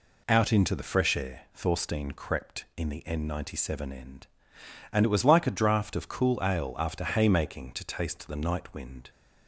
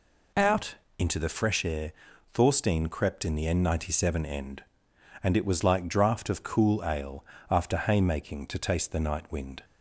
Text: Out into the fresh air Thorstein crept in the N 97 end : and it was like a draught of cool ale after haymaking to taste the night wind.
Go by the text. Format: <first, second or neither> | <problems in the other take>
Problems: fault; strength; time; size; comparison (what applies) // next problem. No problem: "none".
first | pauses between "Out" and "into"; slight; at 0.7 s; 0.20 s long // pauses between "air" and "Thorstein"; at 1.9 s; 0.40 s long // skips "a"; at 5.8 s // pauses between "ale" and "after"; slight; at 7.2 s; 0.28 s long